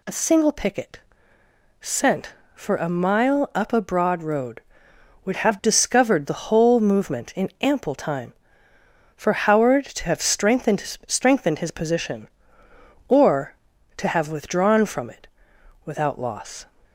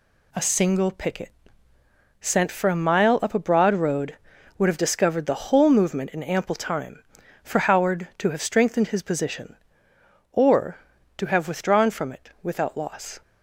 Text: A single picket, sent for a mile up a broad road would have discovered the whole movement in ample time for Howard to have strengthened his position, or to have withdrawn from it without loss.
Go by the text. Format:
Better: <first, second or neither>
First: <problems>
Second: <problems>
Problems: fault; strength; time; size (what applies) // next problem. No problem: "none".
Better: second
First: says "strengthened" twice; at 11.0 s // pauses between "it" and "without"; noticeable; at 15.2 s; 0.58 s long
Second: none